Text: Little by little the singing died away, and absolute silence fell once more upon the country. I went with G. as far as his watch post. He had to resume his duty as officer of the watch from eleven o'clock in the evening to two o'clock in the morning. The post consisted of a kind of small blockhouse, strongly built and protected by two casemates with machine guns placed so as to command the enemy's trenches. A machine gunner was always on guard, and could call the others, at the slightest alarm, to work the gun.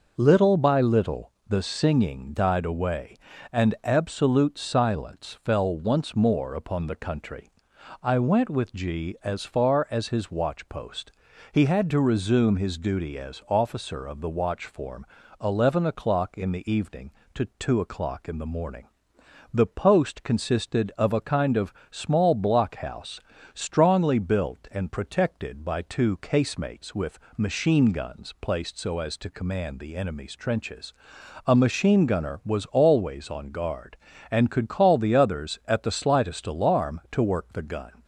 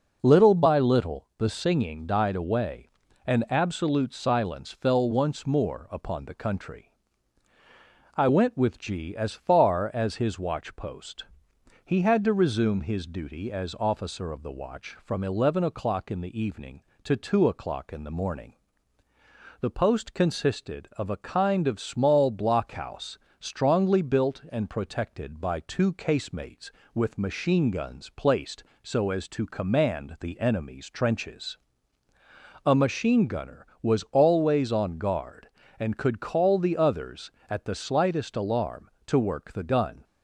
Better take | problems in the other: second | pauses between "little" and "the"; slight; at 1.3 s; 0.16 s long // says "form" for "from"; at 14.6 s // pauses between "of" and "small"; slight; at 21.7 s; 0.16 s long // pauses between "with" and "machine"; slight; at 27.1 s; 0.18 s long

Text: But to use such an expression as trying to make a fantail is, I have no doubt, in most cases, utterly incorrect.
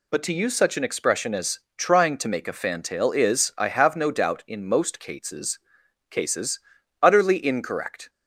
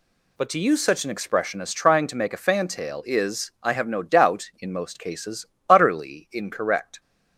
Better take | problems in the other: second | pauses between "as" and "trying"; slight; at 1.5 s; 0.18 s long // says "cases" twice; at 6.0 s

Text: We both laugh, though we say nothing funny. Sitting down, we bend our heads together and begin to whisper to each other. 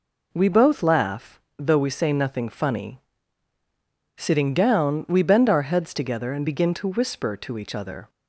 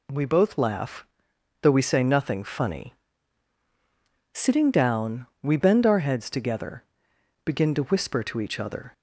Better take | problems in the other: first | skips "and"; at 7.1 s

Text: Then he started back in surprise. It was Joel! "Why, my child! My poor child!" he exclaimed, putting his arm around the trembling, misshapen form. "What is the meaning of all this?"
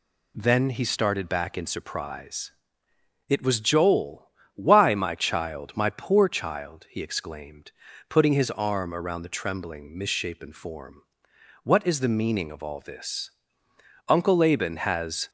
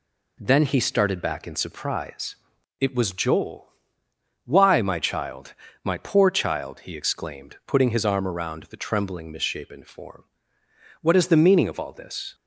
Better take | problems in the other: second | goes on to say "Uncle Laban has"; noticeable; from 14.0 s on; 1.2 s long

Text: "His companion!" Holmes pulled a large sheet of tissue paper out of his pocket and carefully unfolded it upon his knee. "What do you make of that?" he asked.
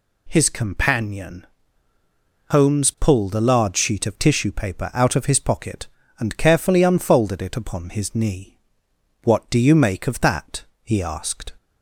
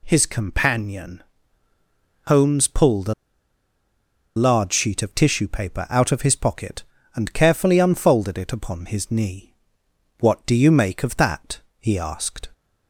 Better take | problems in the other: first | pauses between "a" and "large"; at 3.1 s; 1.2 s long

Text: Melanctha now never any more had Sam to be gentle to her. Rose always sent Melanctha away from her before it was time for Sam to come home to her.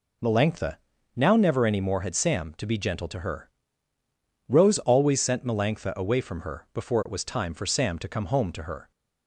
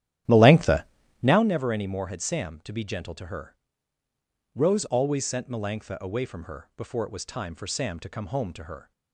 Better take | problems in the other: first | starts louder than the rest; strong; until 1.5 s; 11.5 dB // pauses between "Melanctha" and "now"; slight; at 0.8 s; 0.36 s long; slight in the first

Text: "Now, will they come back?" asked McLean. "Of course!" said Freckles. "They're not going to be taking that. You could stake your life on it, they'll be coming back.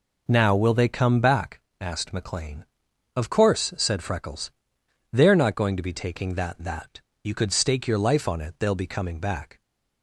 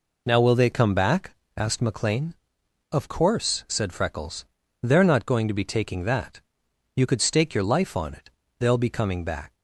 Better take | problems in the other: second | says "that" twice; at 6.5 s

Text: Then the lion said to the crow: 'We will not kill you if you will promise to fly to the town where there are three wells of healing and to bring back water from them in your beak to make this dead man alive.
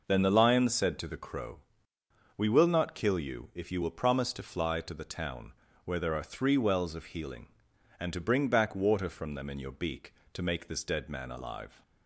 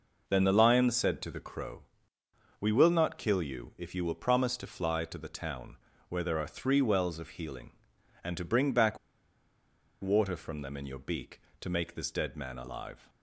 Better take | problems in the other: first | pauses between "town" and "where"; slight; at 5.7 s; 0.32 s long; slight in the first // pauses between "back" and "water"; at 8.9 s; 1.0 s long

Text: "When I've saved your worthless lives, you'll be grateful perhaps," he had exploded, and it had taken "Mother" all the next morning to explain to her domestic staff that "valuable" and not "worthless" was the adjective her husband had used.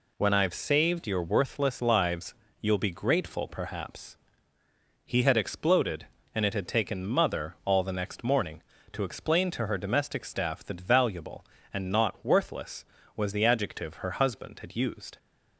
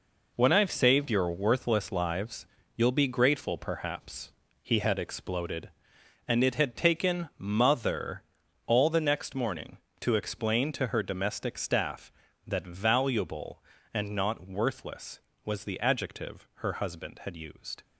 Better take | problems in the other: first | gets quieter; strong; throughout; 8.5 dB // pauses between "Mother" and "all"; at 8.2 s; 0.42 s long // pauses between "adjective" and "her"; slight; at 16.4 s; 0.18 s long

